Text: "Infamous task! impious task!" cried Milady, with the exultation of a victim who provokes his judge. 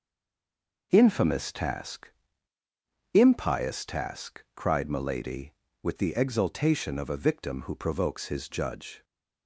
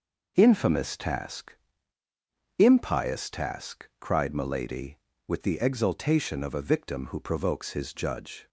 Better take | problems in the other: second | stays silent before the first word; slight; until 0.9 s; 0.9 s long

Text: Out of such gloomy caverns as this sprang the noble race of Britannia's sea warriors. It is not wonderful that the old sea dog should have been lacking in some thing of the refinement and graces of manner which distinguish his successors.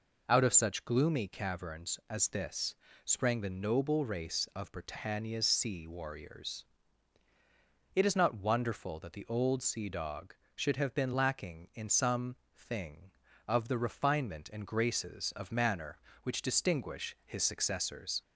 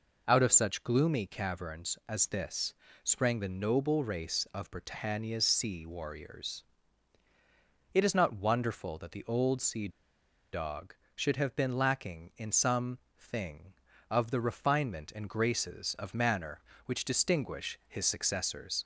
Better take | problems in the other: first | pauses between "this" and "sprang"; slight; at 2.7 s; 0.28 s long; slight in the first // pauses between "sea" and "dog"; noticeable; at 9.8 s; 0.64 s long // pauses between "some" and "thing"; slight; at 12.9 s; 0.18 s long; slight in the first

